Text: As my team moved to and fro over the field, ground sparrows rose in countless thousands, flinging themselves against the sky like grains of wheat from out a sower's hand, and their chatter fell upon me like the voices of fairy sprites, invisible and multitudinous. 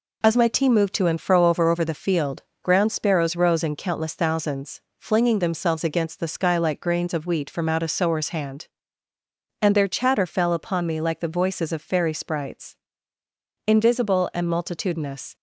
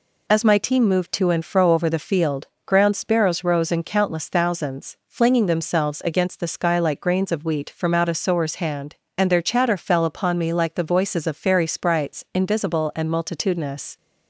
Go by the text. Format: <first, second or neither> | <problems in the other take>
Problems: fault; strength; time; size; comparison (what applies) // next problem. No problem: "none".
second | says "over" twice; at 1.6 s